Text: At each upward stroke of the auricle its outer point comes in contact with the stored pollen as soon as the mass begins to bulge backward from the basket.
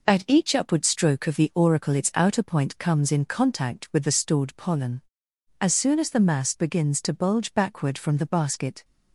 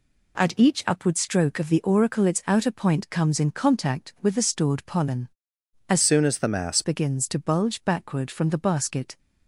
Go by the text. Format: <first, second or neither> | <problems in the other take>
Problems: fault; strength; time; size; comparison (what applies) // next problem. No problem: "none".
first | changes voice from "soon" to "mass"; from 6.0 to 6.8 s; 0.8 s long